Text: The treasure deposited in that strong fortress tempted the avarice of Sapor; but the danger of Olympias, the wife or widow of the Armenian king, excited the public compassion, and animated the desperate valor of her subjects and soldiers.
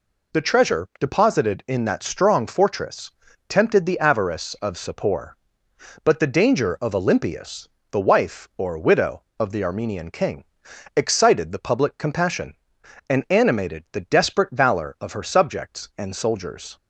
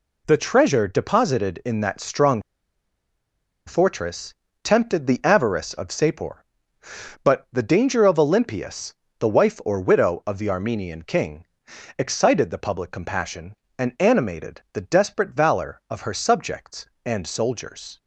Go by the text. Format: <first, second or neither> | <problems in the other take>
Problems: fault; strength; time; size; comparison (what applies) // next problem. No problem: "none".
first | pauses between "strong" and "fortress"; strong; at 2.3 s; 1.2 s long // pauses between "fortress" and "tempted"; slight; at 4.3 s; 0.28 s long; also in the first